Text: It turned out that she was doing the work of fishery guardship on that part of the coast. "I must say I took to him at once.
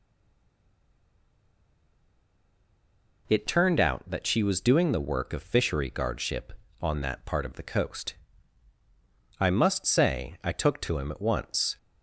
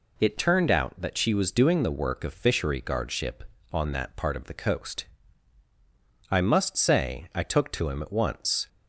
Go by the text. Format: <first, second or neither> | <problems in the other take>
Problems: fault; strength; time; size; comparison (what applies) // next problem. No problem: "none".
second | stays silent before the first word; strong; until 3.2 s; 3.2 s long